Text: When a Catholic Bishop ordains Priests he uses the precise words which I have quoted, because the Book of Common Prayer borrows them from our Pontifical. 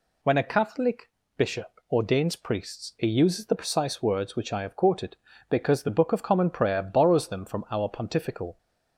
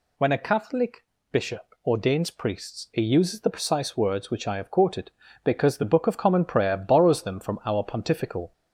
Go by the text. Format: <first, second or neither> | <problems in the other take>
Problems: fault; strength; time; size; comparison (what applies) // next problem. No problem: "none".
first | gets louder; slight; throughout; 2 dB // pauses between "Catholic" and "Bishop"; slight; at 1.0 s; 0.30 s long; slight in the first